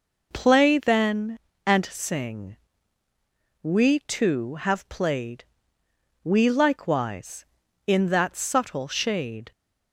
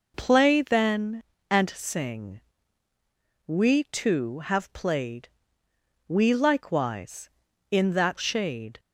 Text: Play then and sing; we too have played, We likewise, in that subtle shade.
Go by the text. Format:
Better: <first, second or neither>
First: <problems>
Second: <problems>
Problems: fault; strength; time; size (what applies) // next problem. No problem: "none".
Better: first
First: none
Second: skips "subtle"; at 8.1 s